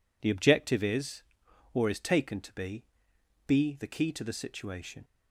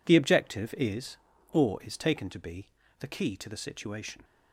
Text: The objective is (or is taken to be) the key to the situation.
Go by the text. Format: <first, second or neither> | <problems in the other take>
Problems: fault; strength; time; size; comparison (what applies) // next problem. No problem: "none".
second | says "be" twice; at 3.4 s